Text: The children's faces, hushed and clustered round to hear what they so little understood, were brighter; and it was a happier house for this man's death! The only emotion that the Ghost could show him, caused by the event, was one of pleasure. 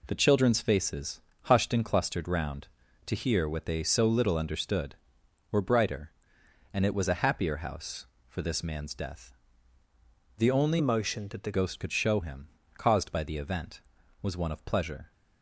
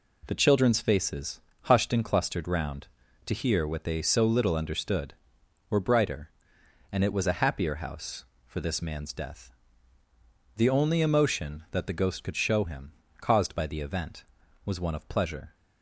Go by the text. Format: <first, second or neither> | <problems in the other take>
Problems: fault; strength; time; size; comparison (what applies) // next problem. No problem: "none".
second | changes voice from "emotion" to "the"; from 10.7 to 11.5 s; 0.8 s long